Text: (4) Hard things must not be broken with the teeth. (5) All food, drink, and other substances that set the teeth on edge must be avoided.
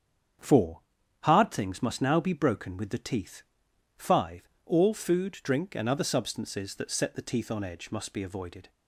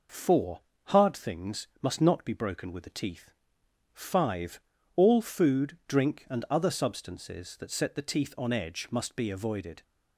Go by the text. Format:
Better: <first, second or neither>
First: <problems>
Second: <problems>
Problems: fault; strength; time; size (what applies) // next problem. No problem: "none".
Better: second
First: starts louder than the rest; strong; until 1.8 s; 8 dB // says "now" for "not"; at 1.9 s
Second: none